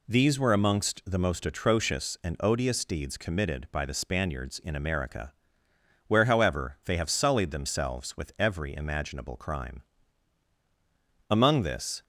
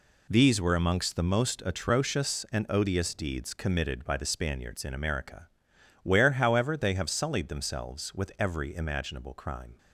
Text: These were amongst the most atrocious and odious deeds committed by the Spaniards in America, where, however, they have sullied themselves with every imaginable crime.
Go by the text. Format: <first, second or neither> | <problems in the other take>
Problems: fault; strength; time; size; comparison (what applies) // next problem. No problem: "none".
second | goes on to say "Among this"; noticeable; from 11.3 s on; 0.72 s long